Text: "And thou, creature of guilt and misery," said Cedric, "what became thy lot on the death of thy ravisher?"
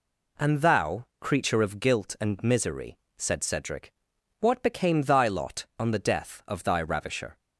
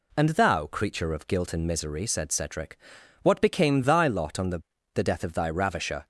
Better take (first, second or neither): first